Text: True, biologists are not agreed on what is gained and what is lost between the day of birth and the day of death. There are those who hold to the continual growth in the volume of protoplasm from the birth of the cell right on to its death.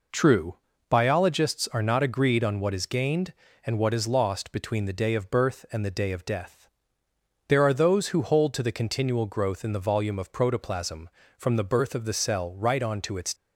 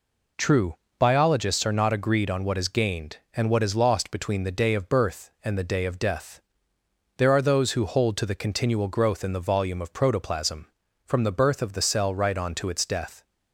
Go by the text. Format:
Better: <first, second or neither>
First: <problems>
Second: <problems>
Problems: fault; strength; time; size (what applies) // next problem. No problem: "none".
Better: second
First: stops before "death"; at 13.3 s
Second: none